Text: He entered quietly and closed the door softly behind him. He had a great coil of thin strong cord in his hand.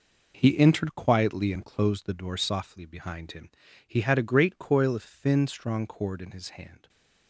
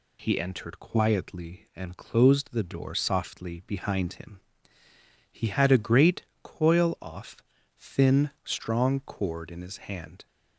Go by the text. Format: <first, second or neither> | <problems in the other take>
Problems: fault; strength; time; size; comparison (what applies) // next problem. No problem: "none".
first | pauses between "great" and "coil"; slight; at 6.2 s; 0.18 s long // says "off" for "of"; at 6.9 s